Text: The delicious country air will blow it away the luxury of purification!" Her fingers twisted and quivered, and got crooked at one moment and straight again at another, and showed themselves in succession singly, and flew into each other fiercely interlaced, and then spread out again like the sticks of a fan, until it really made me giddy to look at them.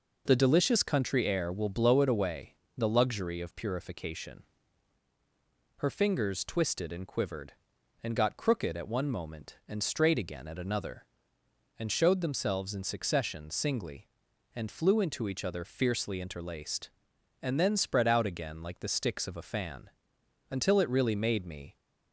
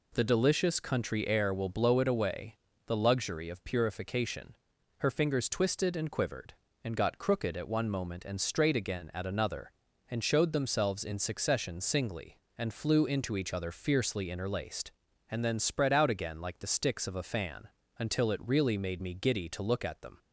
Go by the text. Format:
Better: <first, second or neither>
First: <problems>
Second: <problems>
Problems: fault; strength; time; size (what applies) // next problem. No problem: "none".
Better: second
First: pauses between "away" and "the"; slight; at 2.5 s; 0.22 s long // stops before "giddy to look at them"; at 21.7 s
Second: pauses between "away" and "the"; slight; at 2.5 s; 0.28 s long